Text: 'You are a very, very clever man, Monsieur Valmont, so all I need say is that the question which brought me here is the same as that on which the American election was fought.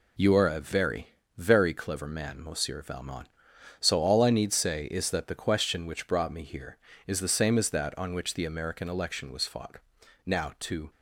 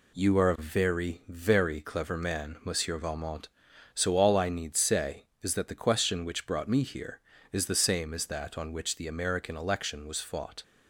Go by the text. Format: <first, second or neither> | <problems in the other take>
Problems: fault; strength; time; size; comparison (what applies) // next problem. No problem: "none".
second | goes on to say "Now to"; noticeable; from 10.2 s on; 0.64 s long